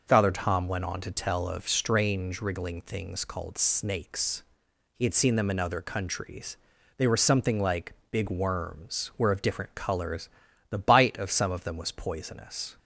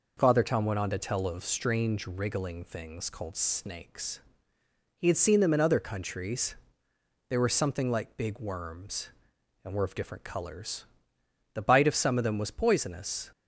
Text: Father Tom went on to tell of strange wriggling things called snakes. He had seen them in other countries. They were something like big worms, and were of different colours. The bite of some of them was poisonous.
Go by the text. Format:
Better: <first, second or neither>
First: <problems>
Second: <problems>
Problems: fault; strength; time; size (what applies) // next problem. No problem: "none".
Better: second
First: pauses between "like" and "big"; slight; at 7.9 s; 0.18 s long // skips "and"; at 9.1 s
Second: none